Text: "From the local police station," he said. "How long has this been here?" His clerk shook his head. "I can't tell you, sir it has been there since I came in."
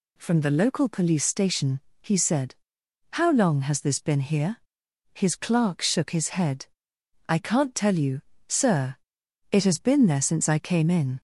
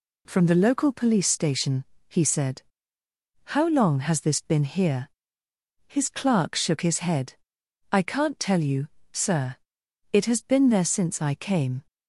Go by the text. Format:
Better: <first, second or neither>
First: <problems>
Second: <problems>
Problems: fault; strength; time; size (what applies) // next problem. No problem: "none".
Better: first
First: pauses between "sir" and "it"; noticeable; at 8.9 s; 0.56 s long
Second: pauses between "sir" and "it"; noticeable; at 9.5 s; 0.56 s long // stops before "in"; at 11.8 s